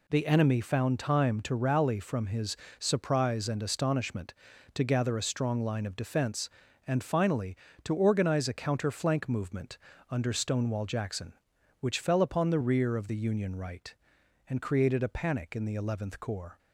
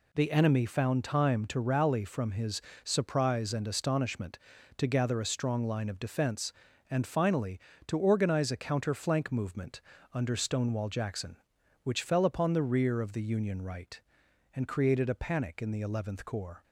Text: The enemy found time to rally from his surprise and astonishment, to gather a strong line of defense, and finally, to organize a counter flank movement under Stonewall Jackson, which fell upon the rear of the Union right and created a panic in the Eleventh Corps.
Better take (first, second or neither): neither